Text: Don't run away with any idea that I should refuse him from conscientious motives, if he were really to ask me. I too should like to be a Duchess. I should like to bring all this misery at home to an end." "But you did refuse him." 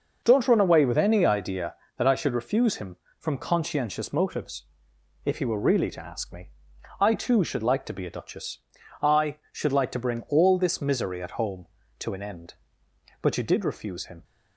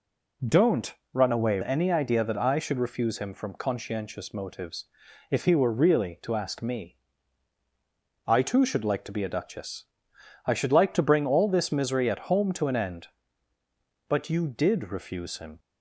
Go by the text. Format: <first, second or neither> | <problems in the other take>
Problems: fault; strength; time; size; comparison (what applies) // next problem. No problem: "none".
first | pauses between "Don't" and "run"; slight; at 0.9 s; 0.18 s long // skips "with"; at 1.6 s